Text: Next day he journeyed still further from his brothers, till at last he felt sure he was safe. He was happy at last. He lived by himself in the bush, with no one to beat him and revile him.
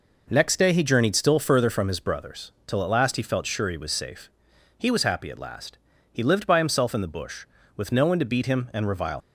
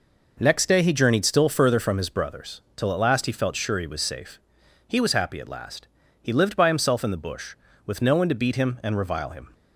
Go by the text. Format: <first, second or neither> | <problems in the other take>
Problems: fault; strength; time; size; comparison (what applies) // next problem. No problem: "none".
second | stops before "him"; at 9.2 s